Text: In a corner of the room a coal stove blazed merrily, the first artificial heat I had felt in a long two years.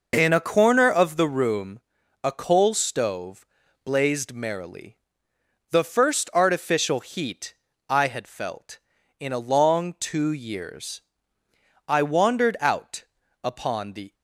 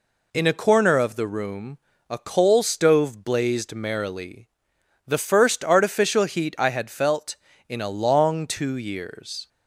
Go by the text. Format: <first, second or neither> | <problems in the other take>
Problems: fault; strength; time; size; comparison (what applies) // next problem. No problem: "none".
second | pauses between "room" and "a"; at 1.8 s; 0.42 s long; slight in the second // pauses between "stove" and "blazed"; at 3.4 s; 0.40 s long // pauses between "heat" and "I"; slight; at 7.5 s; 0.34 s long // goes on to say "I wandered out upon the"; strong; from 11.8 s on; 2.2 s long